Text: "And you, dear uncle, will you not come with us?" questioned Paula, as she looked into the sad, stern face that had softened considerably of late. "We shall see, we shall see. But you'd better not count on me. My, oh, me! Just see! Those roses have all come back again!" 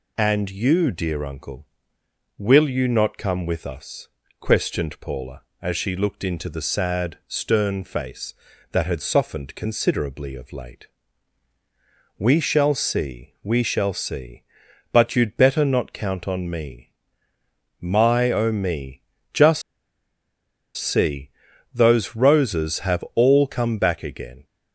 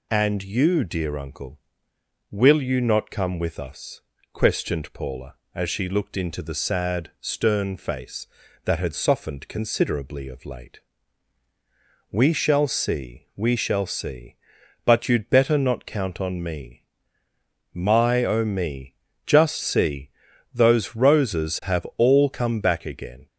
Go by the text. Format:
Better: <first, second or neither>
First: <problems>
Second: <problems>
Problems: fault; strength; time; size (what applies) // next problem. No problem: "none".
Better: second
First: pauses between "Just" and "see"; at 19.6 s; 1.1 s long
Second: none